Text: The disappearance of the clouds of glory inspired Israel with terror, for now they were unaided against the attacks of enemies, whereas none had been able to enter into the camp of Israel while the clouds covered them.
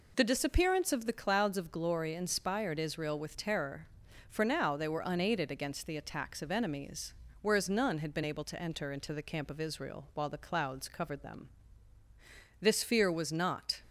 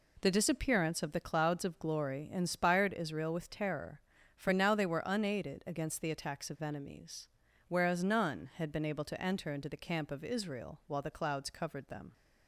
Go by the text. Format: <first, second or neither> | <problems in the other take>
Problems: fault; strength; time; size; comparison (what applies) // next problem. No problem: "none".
second | goes on to say "This fear was not"; noticeable; from 12.6 s on; 1.2 s long